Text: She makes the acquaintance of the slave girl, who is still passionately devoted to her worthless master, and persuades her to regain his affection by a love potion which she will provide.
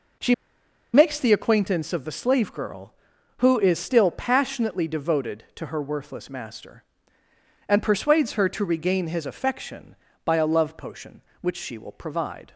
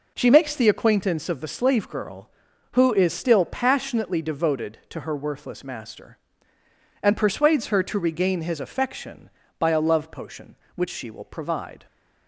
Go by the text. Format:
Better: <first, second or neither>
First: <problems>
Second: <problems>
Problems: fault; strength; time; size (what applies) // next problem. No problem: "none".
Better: second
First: pauses between "She" and "makes"; noticeable; at 0.3 s; 0.59 s long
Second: none